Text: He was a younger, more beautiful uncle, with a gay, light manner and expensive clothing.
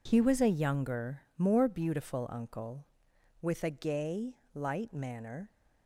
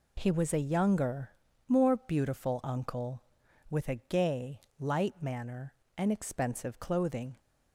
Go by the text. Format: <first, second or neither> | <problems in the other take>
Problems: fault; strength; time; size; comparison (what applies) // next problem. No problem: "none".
second | stops before "and expensive clothing"; at 5.5 s